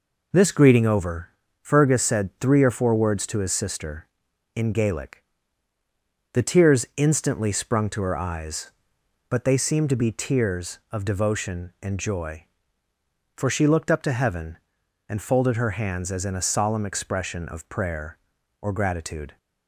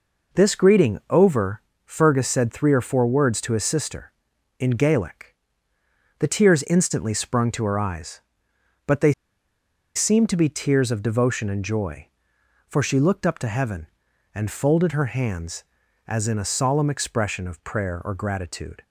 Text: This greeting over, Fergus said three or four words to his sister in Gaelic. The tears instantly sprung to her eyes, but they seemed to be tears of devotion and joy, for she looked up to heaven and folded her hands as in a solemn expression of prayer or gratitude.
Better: first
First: none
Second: pauses between "they" and "seemed"; noticeable; at 9.1 s; 0.84 s long

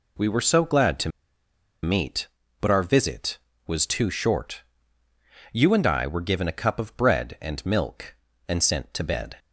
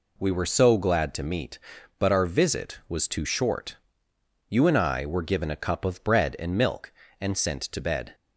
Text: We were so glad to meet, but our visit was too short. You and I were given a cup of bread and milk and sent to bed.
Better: second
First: pauses between "to" and "meet"; noticeable; at 1.0 s; 0.73 s long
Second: none

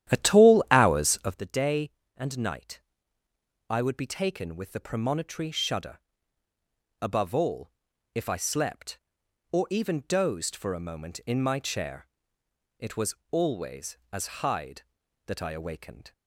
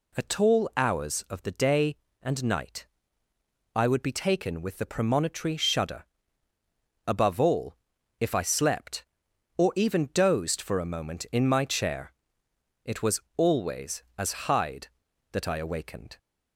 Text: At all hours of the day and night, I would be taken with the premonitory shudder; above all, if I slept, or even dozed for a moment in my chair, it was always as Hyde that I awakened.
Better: second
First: starts louder than the rest; strong; until 1.4 s; 11.5 dB // pauses between "was" and "always"; slight; at 13.1 s; 0.16 s long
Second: pauses between "was" and "always"; slight; at 13.1 s; 0.16 s long

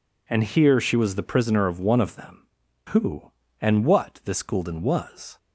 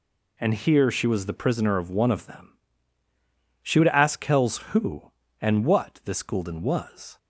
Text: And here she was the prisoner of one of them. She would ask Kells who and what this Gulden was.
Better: second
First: skips "She would ask Kells"; at 2.6 s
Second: none

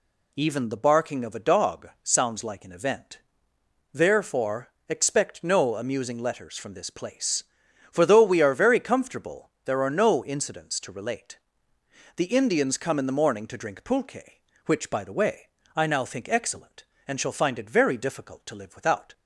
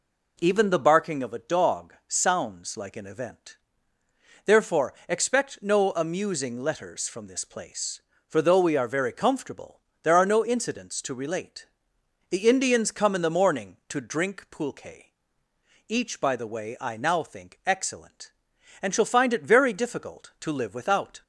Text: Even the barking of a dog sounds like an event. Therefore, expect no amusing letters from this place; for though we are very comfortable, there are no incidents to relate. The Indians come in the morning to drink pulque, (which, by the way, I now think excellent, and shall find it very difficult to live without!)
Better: first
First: none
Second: says "each" for "which"; at 15.8 s

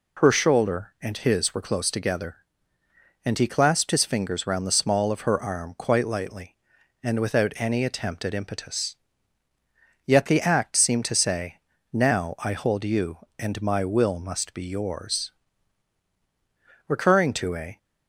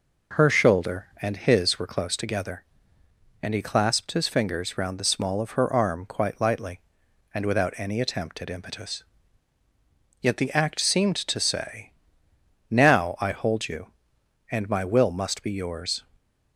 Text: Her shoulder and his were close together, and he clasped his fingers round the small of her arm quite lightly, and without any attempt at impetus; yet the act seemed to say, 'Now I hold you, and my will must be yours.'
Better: second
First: goes on to say "Recurring to a"; noticeable; from 16.8 s on; 0.90 s long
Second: none

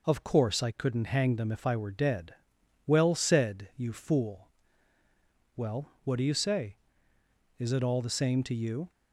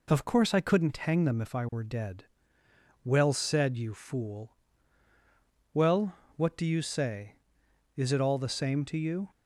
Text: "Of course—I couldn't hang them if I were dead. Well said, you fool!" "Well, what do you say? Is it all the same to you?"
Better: neither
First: none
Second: none

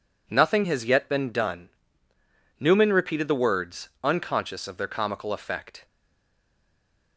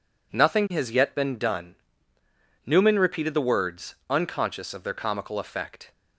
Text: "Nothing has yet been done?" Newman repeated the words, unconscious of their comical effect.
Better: second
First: stays silent after the last word; noticeable; from 5.8 s on; 1.3 s long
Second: none

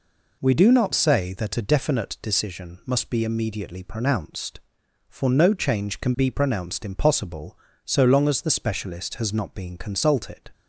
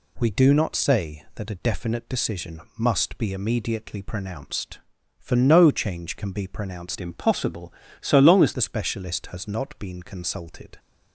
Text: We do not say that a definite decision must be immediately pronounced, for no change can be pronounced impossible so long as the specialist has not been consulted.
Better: first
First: none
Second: pauses between "decision" and "must"; slight; at 2.6 s; 0.16 s long // changes voice from "impossible" to "as"; from 7.0 to 8.5 s; 1.5 s long

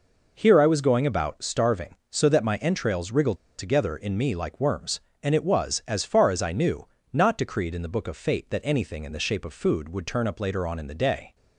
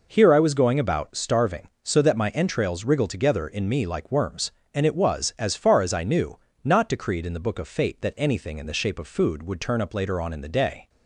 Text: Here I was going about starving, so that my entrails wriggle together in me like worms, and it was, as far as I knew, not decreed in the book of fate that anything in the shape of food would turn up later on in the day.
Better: second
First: pauses between "wriggle" and "together"; slight; at 3.3 s; 0.23 s long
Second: none

